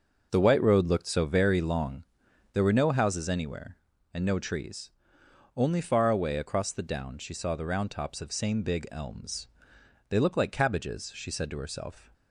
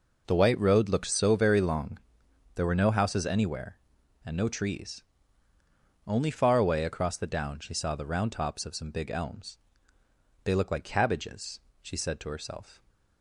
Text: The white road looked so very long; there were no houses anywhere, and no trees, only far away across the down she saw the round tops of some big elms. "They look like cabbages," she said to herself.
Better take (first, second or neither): second